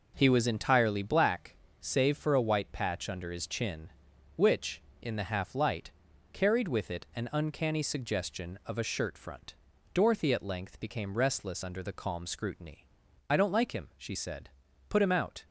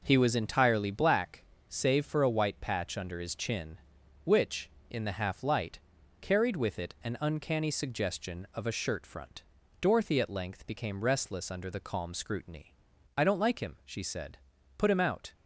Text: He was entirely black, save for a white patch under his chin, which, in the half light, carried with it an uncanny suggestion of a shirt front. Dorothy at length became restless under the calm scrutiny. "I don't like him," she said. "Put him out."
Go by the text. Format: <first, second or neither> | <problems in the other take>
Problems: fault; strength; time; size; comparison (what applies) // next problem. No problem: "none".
neither | none